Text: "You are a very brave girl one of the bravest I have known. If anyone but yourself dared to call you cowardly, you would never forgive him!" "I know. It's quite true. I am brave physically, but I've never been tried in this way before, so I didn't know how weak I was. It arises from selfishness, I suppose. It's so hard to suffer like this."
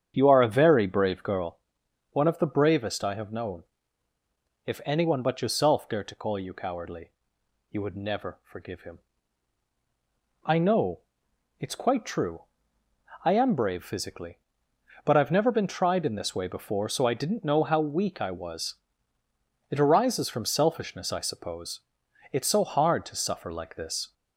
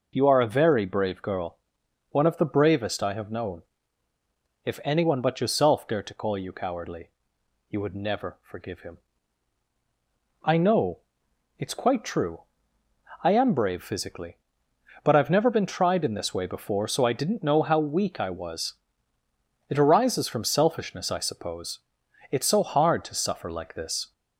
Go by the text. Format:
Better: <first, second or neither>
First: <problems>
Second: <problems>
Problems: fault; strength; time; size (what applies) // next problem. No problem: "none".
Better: second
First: starts louder than the rest; strong; until 1.6 s; 8 dB // pauses between "girl" and "one"; noticeable; at 1.5 s; 0.52 s long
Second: pauses between "girl" and "one"; noticeable; at 1.5 s; 0.52 s long